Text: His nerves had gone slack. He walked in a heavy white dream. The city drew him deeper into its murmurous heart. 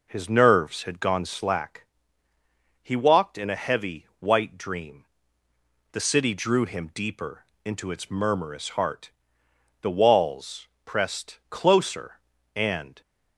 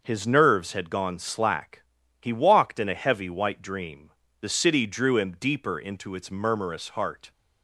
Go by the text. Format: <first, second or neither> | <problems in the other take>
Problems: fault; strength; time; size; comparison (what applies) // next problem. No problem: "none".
second | pauses between "deeper" and "into"; slight; at 7.4 s; 0.18 s long // goes on to say "The walls pressed closer and"; strong; from 9.8 s on; 3.1 s long